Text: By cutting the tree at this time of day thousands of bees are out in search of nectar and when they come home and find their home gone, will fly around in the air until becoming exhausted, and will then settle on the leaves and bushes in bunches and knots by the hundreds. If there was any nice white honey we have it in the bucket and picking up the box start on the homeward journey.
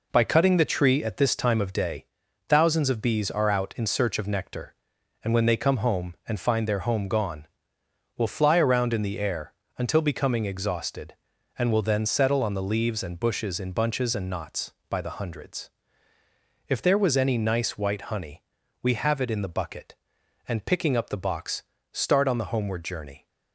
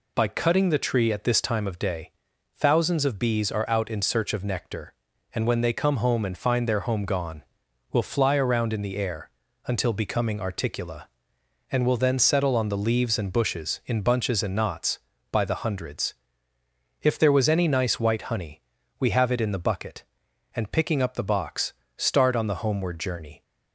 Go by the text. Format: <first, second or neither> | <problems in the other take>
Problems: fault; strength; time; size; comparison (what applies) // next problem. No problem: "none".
first | pauses between "day" and "thousands"; noticeable; at 2.1 s; 0.46 s long; also in the first // pauses between "air" and "until"; slight; at 9.3 s; 0.36 s long; slight in the first // says "articula" for "exhausted"; at 10.4 s // pauses between "honey" and "we"; at 18.6 s; 0.38 s long; also in the first // pauses between "box" and "start"; slight; at 21.7 s; 0.24 s long; slight in the first